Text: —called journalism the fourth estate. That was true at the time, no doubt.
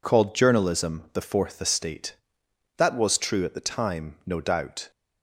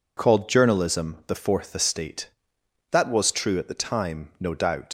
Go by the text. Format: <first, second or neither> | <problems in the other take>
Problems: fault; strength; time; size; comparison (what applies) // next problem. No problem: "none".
first | leaves "doubt" unfinished; at 4.8 s; 115 ms